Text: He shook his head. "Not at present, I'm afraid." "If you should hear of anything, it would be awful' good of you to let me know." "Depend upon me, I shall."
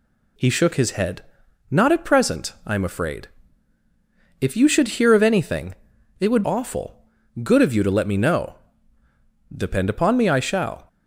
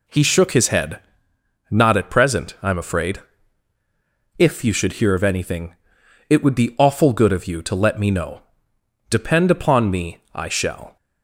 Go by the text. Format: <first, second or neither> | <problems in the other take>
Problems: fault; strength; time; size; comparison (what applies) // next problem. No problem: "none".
second | skips "be"; at 6.4 s // pauses between "awful" and "good"; at 7.0 s; 0.40 s long